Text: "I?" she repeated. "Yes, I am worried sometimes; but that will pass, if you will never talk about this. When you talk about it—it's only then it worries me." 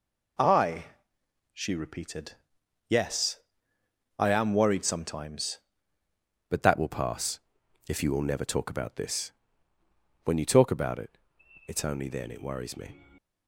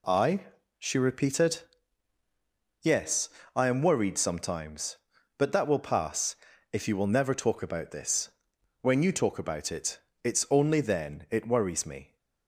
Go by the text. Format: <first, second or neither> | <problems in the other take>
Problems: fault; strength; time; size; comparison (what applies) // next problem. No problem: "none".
second | changes voice at "but"; from 6.4 s on; 6.5 s long